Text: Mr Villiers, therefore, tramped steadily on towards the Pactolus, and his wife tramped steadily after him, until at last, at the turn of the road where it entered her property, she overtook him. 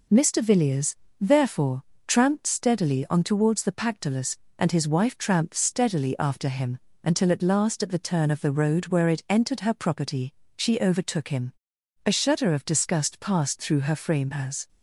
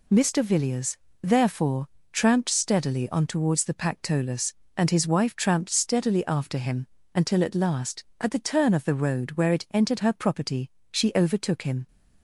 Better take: second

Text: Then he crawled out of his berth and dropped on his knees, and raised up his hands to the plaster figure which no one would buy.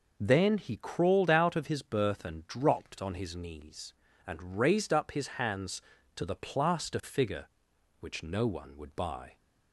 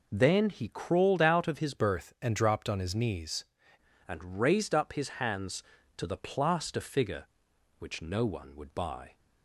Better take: first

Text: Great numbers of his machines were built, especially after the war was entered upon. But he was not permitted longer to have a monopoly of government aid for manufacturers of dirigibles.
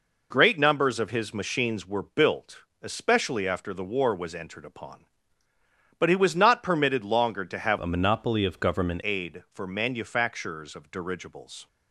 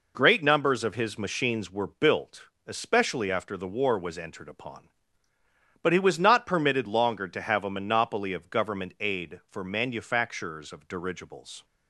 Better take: second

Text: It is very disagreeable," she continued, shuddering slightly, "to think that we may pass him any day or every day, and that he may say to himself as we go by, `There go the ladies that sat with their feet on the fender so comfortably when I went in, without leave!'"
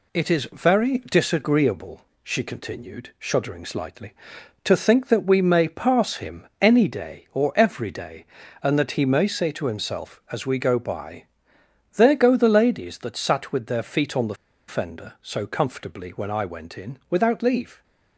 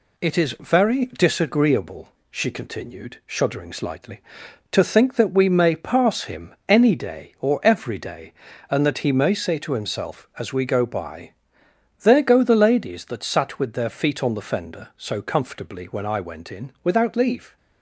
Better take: second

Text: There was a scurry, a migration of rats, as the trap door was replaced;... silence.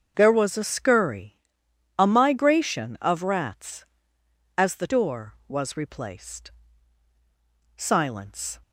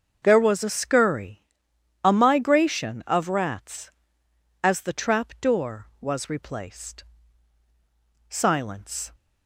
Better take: second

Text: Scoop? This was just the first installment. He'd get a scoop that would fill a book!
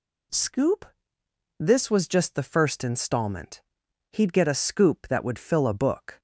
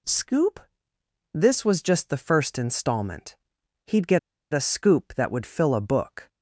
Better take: first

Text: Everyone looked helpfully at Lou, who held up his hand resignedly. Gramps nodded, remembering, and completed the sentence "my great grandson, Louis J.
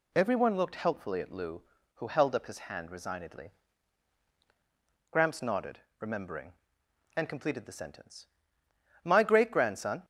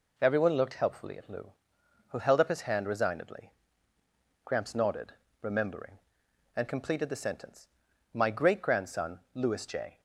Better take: second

